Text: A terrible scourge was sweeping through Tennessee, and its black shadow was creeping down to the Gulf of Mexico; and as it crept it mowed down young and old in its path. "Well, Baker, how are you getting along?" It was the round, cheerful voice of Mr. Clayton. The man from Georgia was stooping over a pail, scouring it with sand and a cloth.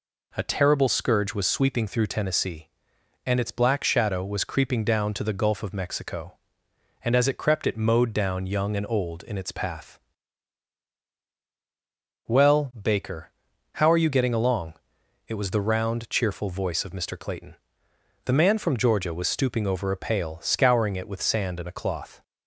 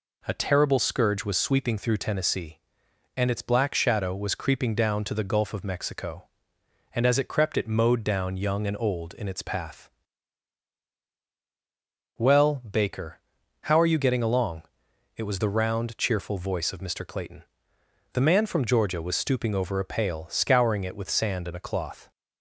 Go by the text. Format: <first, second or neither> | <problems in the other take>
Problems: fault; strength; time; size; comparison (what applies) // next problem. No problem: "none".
neither | none